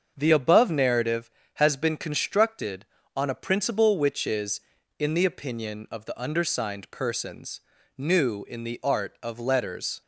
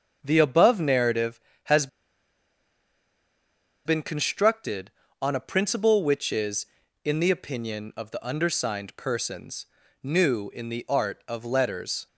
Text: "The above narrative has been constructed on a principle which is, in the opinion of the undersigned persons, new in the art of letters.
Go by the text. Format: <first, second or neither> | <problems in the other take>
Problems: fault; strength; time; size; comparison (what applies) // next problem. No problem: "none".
first | starts louder than the rest; until 1.2 s; 7 dB; also in the first // pauses between "has" and "been"; strong; at 1.8 s; 1.9 s long